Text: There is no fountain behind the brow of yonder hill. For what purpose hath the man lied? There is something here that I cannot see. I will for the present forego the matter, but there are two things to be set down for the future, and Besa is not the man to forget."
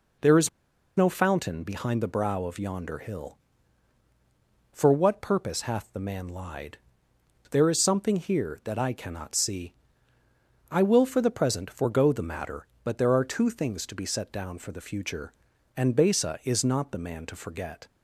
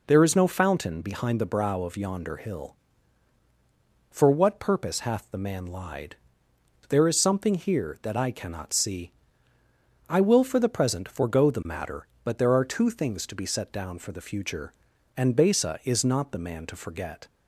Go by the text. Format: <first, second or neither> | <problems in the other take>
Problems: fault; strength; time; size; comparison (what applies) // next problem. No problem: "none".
second | pauses between "is" and "no"; noticeable; at 0.4 s; 0.48 s long